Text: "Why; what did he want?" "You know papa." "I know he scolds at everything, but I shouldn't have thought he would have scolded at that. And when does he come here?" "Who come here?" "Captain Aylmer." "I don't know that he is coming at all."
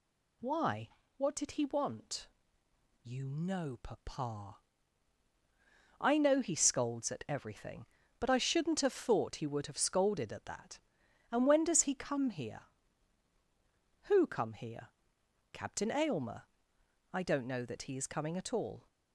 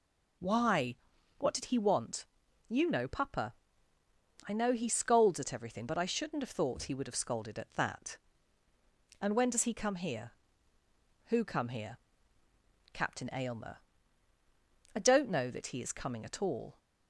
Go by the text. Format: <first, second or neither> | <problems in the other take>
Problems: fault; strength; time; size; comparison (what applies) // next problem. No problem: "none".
neither | none